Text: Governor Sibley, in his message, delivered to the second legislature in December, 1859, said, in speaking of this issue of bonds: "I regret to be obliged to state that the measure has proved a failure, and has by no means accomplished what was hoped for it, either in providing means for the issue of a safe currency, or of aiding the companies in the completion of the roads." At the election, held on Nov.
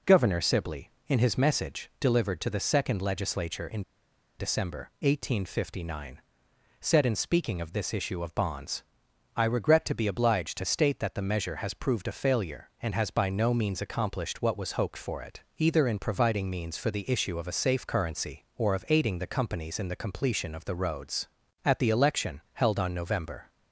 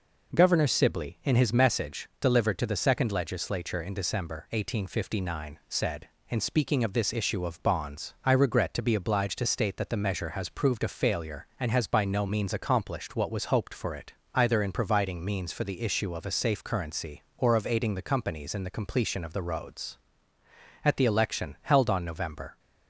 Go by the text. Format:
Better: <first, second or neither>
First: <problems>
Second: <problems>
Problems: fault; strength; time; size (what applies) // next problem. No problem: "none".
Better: second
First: pauses between "in" and "December"; noticeable; at 3.8 s; 0.57 s long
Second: none